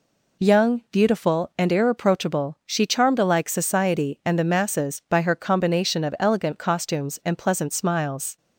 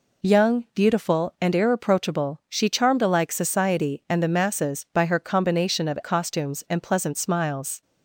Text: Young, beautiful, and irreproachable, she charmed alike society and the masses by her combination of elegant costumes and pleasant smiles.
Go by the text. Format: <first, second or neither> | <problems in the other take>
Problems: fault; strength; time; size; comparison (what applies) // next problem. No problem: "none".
first | skips "elegant"; at 6.0 s